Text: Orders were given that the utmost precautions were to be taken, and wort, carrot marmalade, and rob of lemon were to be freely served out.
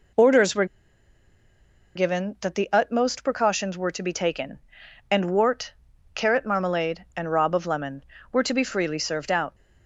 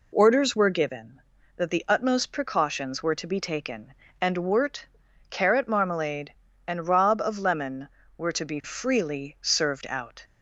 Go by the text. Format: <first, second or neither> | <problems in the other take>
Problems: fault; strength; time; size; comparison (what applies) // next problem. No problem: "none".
second | pauses between "were" and "given"; strong; at 0.6 s; 1.3 s long